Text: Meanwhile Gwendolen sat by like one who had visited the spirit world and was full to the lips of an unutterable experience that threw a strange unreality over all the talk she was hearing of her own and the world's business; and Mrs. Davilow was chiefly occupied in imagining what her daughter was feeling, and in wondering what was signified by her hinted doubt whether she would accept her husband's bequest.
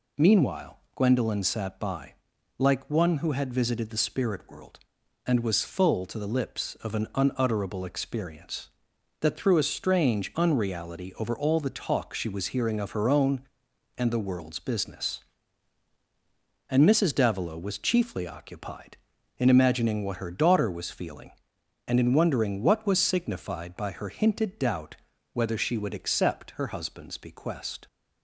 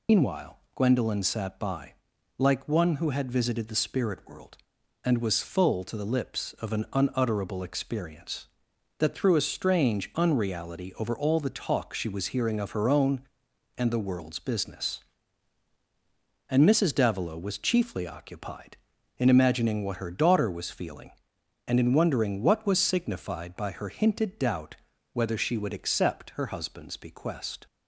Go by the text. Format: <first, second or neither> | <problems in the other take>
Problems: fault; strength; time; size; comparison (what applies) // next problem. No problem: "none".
first | loses the start of "Meanwhile"; at 0.0 s; 120 ms // pauses between "Meanwhile" and "Gwendolen"; slight; at 0.5 s; 0.16 s long; slight in the first // pauses between "by" and "like"; at 1.9 s; 0.44 s long; also in the first // pauses between "doubt" and "whether"; at 24.7 s; 0.38 s long; also in the first